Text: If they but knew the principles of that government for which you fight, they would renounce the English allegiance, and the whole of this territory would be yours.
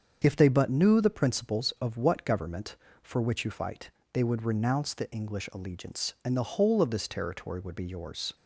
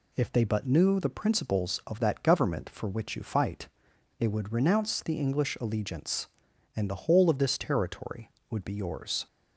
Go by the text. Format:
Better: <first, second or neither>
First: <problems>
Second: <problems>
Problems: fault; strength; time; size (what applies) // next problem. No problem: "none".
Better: second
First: starts louder than the rest; until 1.2 s; 7 dB // says "what" for "that"; at 1.9 s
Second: none